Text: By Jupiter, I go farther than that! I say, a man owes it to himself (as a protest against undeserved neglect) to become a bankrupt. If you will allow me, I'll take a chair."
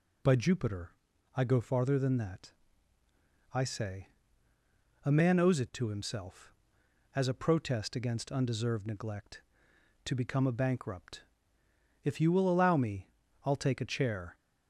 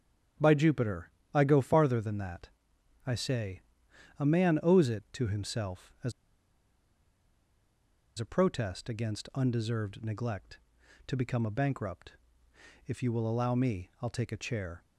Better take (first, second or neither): first